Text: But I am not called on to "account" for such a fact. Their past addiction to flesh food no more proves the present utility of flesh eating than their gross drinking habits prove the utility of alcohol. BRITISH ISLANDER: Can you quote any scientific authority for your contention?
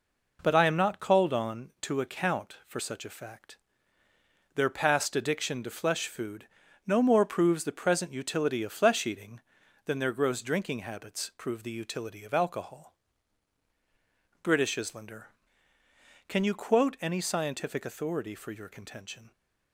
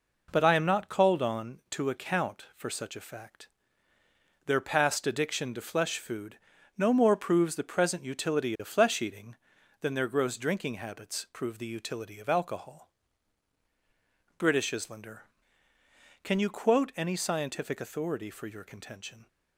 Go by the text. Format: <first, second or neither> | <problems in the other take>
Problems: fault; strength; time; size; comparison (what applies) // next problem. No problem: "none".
neither | pauses between "food" and "no"; the same in both